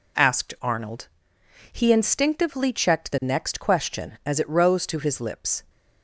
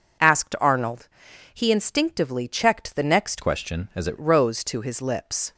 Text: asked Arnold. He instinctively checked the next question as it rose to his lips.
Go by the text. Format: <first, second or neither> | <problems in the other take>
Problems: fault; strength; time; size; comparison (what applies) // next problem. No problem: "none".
first | changes voice from "question" to "it"; from 3.4 to 4.1 s; 0.7 s long